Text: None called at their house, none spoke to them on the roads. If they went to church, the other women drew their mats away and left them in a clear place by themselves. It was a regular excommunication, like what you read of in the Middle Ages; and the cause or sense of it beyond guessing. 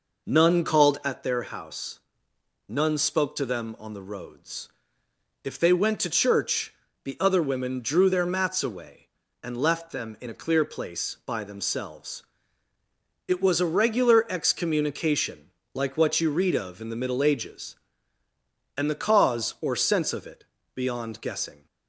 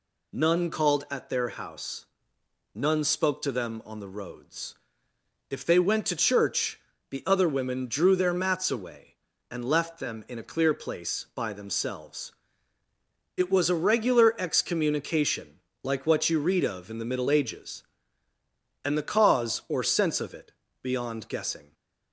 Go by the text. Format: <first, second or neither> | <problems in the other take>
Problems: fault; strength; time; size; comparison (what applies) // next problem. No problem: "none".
second | starts louder than the rest; noticeable; until 1.3 s; 5 dB // pauses between "it" and "beyond"; slight; at 20.4 s; 0.28 s long; slight in the second